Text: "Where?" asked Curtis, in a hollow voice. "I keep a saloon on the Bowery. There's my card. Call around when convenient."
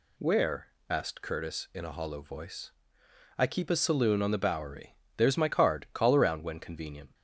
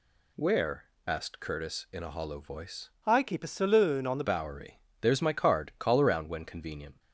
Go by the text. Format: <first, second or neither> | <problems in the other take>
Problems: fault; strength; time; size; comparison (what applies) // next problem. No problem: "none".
first | changes voice from "I" to "the"; from 3.0 to 4.2 s; 1.2 s long